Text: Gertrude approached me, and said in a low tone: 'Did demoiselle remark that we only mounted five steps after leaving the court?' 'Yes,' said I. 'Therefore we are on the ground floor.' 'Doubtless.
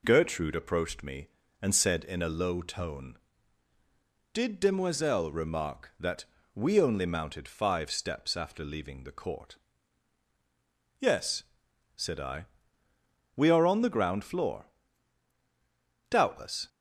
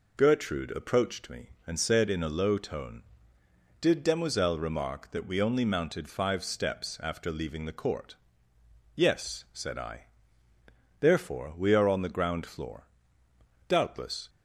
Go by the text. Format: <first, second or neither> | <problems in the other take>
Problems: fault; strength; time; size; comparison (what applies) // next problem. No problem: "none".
second | pauses between "that" and "we"; slight; at 6.2 s; 0.28 s long // skips "Therefore"; at 12.8 s